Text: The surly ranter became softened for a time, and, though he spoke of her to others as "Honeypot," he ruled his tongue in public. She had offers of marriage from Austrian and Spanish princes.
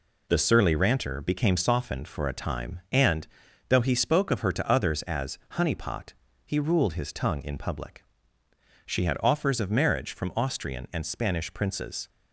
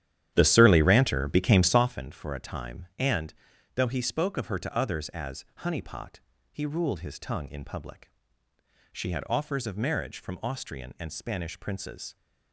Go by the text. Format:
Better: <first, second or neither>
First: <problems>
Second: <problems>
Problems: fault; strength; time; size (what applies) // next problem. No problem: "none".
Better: first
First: none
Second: starts louder than the rest; strong; until 2.0 s; 11 dB